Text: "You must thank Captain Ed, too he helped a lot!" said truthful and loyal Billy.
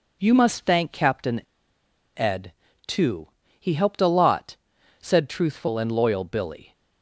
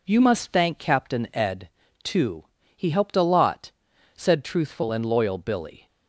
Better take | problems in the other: second | pauses between "Captain" and "Ed"; noticeable; at 1.4 s; 0.76 s long // pauses between "too" and "he"; slight; at 3.2 s; 0.32 s long; slight in the second

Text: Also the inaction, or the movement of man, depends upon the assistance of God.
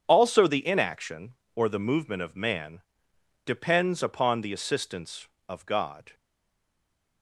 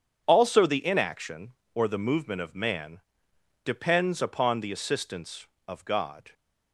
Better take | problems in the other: second | starts louder than the rest; strong; until 1.0 s; 8 dB; strong in the second // stays silent after the last word; from 6.1 s on; 1.1 s long

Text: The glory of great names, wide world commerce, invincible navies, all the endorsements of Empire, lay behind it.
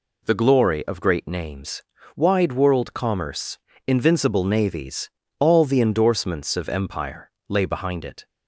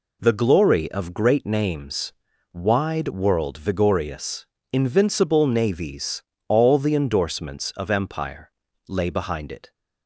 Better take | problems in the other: first | says "vigorious" for "commerce"; at 3.5 s

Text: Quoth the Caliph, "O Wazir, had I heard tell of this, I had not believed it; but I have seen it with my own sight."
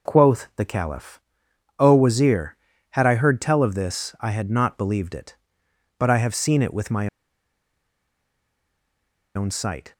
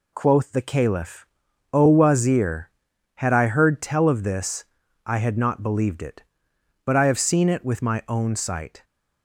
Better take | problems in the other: second | pauses between "my" and "own"; strong; at 7.0 s; 2.2 s long

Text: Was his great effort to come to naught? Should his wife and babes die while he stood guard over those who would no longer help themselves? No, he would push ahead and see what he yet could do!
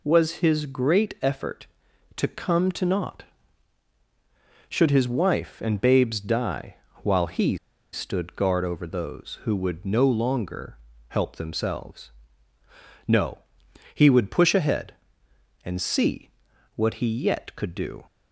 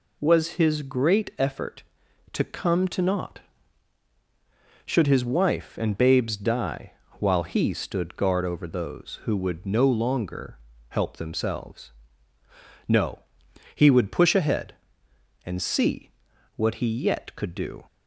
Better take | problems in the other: second | pauses between "die" and "while"; slight; at 6.7 s; 0.30 s long; slight in the second // pauses between "he" and "stood"; at 7.5 s; 0.36 s long // pauses between "longer" and "help"; slight; at 10.7 s; 0.30 s long; slight in the second // pauses between "see" and "what"; noticeable; at 16.2 s; 0.46 s long; noticeable in the second

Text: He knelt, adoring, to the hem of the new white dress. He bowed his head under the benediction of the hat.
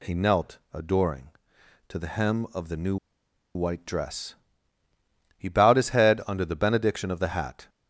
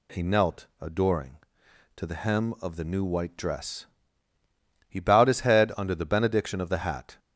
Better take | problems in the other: second | pauses between "new" and "white"; noticeable; at 2.9 s; 0.58 s long

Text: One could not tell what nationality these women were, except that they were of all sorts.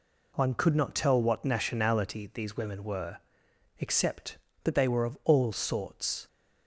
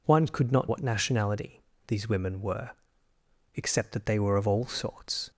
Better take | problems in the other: first | skips "tell"; at 0.6 s // pauses between "nationality" and "these"; slight; at 1.6 s; 0.24 s long

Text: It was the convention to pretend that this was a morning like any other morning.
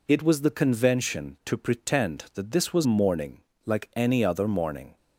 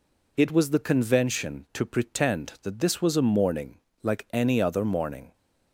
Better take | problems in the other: second | skips "a"; at 2.8 s // pauses between "morning" and "like"; slight; at 3.4 s; 0.22 s long; slight in the second

